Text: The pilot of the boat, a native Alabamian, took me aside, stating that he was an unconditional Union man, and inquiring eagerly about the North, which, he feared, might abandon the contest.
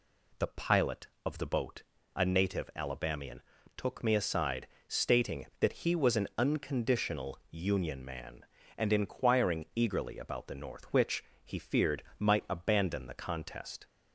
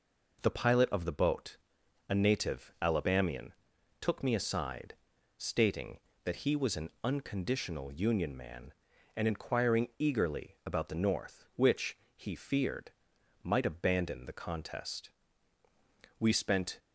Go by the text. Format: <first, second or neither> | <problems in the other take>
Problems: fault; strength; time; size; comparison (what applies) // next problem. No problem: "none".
first | pauses between "an" and "unconditional"; slight; at 6.8 s; 0.16 s long // goes on to say "We spent"; from 16.2 s on; 0.58 s long